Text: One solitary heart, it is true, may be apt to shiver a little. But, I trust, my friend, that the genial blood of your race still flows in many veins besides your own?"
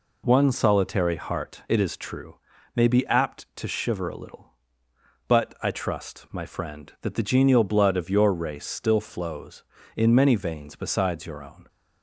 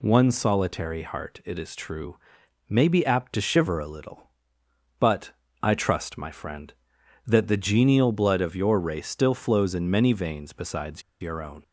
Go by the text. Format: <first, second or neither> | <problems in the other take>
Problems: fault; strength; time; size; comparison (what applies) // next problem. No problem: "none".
first | pauses between "besides" and "your"; slight; at 11.0 s; 0.20 s long